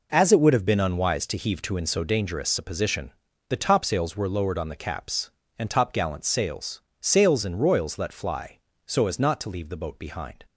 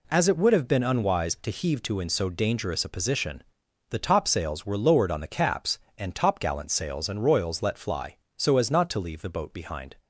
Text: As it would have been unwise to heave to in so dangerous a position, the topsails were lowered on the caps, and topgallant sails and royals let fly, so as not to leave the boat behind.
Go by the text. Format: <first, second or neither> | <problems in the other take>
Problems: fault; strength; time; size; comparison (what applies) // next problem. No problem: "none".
second | says "sails" twice; at 6.9 s